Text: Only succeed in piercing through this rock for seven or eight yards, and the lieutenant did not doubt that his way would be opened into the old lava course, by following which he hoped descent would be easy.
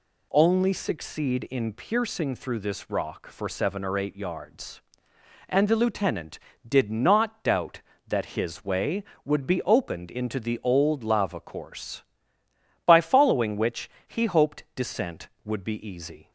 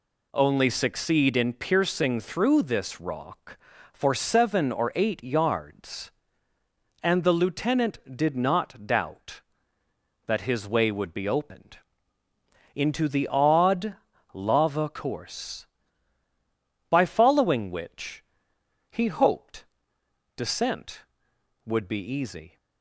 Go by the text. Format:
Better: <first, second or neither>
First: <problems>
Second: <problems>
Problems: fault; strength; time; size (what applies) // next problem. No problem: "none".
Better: first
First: pauses between "which" and "he"; slight; at 13.8 s; 0.16 s long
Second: pauses between "opened" and "into"; noticeable; at 11.7 s; 0.96 s long // says "odd" for "old"; at 13.2 s // pauses between "which" and "he"; noticeable; at 18.2 s; 0.66 s long // pauses between "hoped" and "descent"; noticeable; at 19.6 s; 0.72 s long